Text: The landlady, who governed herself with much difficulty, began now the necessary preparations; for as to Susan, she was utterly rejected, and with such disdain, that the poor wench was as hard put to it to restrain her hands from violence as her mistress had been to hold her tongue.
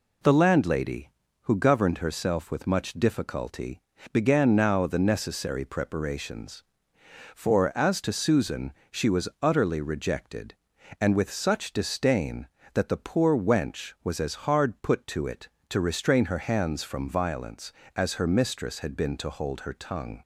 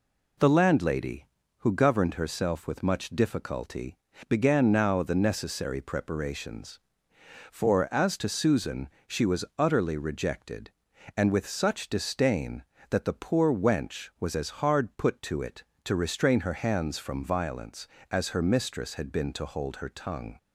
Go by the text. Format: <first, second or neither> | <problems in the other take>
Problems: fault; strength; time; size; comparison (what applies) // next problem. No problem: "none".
neither | pauses between "was" and "utterly"; slight; the same in both